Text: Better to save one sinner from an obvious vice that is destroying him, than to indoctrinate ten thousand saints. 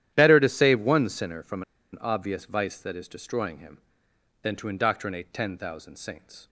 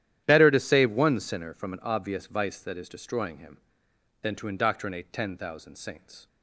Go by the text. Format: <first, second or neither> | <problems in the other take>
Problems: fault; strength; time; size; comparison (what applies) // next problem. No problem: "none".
second | starts louder than the rest; strong; until 1.1 s; 11.5 dB; strong in the second // pauses between "from" and "an"; slight; at 1.6 s; 0.29 s long